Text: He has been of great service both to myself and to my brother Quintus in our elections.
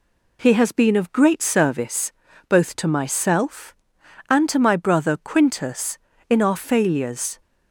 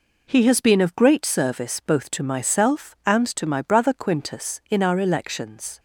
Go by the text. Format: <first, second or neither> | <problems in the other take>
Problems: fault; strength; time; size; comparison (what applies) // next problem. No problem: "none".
second | pauses between "service" and "both"; slight; at 2.1 s; 0.36 s long // says "failures" for "elections"; at 6.5 s